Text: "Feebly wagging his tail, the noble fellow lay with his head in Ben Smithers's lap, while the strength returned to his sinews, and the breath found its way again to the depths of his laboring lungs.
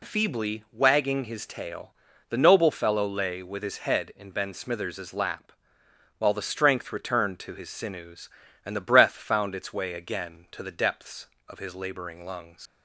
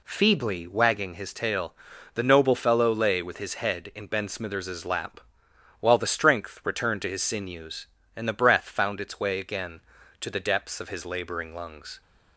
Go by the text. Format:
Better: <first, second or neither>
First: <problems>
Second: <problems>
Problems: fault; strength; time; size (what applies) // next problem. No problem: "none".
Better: second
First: leaves "lungs" unfinished; at 12.6 s; 95 ms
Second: none